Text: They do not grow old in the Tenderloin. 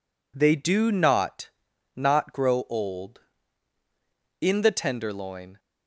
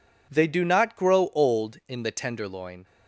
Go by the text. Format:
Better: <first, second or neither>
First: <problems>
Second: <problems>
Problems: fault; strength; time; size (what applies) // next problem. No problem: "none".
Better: second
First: says "not" twice; at 1.9 s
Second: none